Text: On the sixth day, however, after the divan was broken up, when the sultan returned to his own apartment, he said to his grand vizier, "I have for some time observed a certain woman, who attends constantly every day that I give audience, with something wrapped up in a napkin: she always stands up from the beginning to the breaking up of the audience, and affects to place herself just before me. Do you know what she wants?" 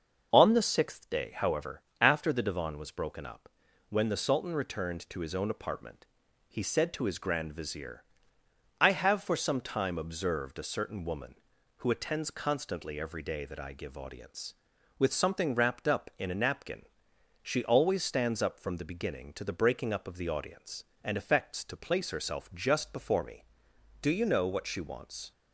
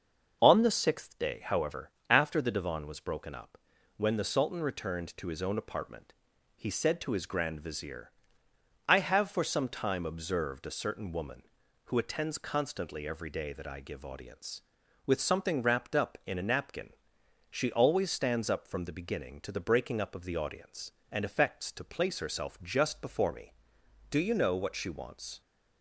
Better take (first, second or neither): neither